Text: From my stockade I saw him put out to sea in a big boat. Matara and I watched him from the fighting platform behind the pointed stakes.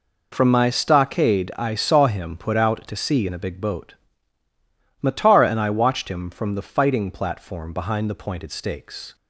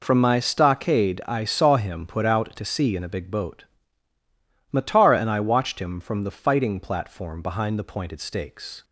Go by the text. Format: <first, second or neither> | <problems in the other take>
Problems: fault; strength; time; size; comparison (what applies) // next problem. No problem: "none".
neither | none